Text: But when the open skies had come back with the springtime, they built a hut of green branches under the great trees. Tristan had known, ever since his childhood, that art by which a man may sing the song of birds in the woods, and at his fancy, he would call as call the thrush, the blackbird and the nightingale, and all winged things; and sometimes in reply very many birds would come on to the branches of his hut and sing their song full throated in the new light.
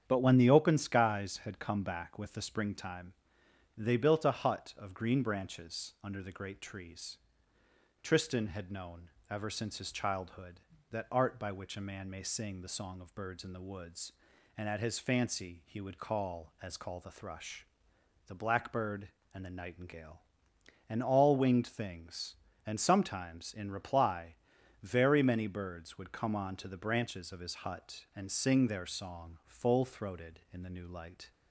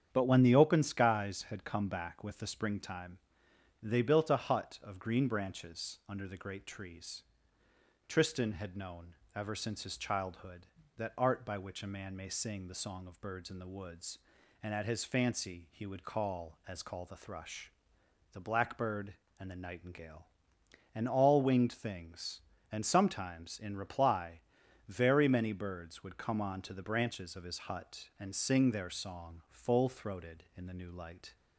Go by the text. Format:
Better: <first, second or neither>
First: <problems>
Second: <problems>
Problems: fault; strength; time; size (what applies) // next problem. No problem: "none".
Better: neither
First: starts louder than the rest; strong; until 1.0 s; 8.5 dB // pauses between "reply" and "very"; noticeable; at 24.3 s; 0.48 s long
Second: starts louder than the rest; strong; until 1.1 s; 8.5 dB // pauses between "reply" and "very"; noticeable; at 24.3 s; 0.48 s long